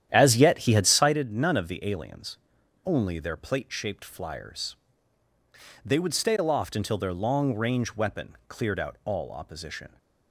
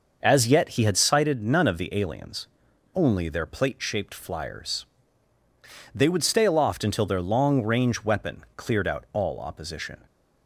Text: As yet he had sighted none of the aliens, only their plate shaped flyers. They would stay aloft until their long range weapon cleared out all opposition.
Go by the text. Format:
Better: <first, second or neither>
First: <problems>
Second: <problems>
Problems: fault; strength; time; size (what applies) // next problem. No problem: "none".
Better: second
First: starts louder than the rest; strong; until 1.2 s; 10.5 dB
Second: none